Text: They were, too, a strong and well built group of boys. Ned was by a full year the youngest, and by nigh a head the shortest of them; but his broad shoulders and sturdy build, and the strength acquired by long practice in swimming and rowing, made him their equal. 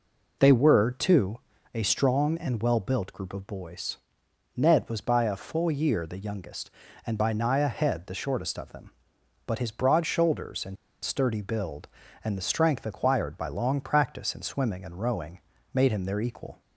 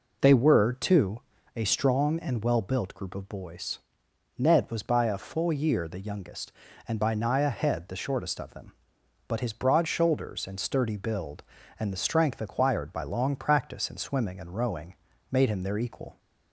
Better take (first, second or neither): second